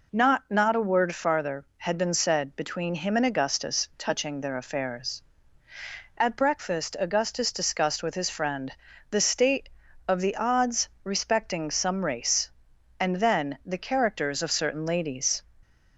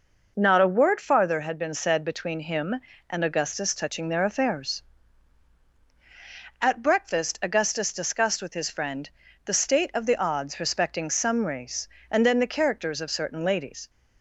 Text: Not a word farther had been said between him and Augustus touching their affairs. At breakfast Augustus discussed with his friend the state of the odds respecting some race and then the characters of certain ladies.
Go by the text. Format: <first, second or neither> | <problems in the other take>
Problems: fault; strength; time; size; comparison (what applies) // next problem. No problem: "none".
second | says "Not" twice; at 0.4 s // pauses between "friend" and "the"; slight; at 8.7 s; 0.36 s long; slight in the second